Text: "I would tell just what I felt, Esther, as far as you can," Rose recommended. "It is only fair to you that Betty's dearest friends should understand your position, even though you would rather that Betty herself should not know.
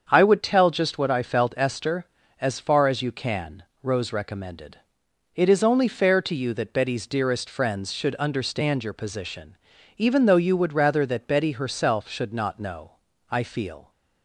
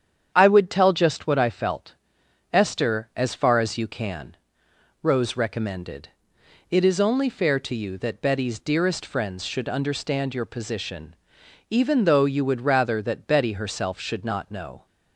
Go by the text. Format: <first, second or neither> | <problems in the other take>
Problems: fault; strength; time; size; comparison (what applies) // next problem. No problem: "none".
second | starts louder than the rest; strong; until 1.0 s; 7 dB; strong in the second // goes on to say "I feel"; noticeable; from 13.2 s on; 0.62 s long